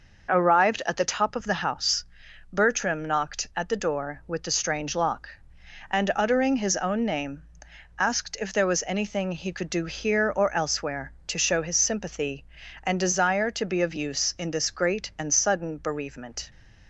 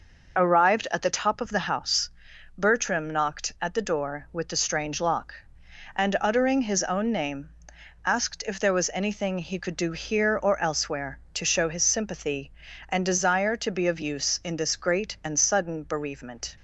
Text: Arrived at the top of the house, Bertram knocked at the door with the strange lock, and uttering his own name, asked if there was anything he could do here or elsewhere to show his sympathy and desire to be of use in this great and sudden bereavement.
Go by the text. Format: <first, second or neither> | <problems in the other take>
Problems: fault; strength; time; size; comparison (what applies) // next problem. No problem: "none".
first | loses the start of "Arrived"; at 0.3 s; 20 ms